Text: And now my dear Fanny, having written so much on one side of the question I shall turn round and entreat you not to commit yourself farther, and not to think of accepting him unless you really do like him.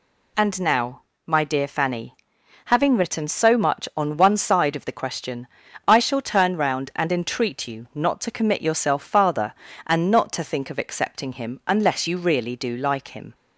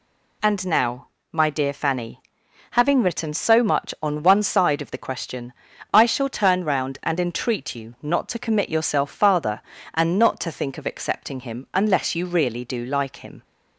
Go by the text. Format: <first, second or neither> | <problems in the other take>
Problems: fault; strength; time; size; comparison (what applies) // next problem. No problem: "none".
neither | pauses between "now" and "my"; slight; the same in both // pauses between "question" and "I"; the same in both